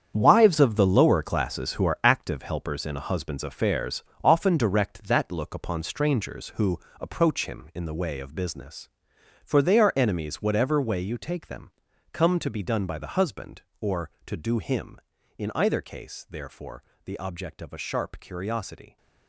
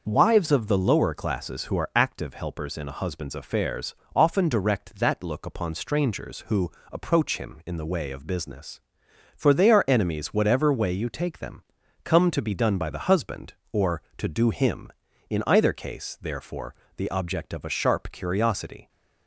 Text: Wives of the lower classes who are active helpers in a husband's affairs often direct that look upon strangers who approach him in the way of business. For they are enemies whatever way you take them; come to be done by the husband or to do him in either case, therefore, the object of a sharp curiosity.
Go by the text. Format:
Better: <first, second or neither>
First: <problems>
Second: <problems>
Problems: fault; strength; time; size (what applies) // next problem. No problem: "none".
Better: second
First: gets quieter; strong; throughout; 10.5 dB // starts louder than the rest; strong; until 1.1 s; 8 dB // pauses between "affairs" and "often"; slight; at 4.0 s; 0.18 s long // pauses between "who" and "approach"; slight; at 6.7 s; 0.22 s long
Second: starts louder than the rest; noticeable; until 1.0 s; 6 dB // pauses between "affairs" and "often"; slight; at 3.9 s; 0.18 s long // pauses between "who" and "approach"; slight; at 6.7 s; 0.22 s long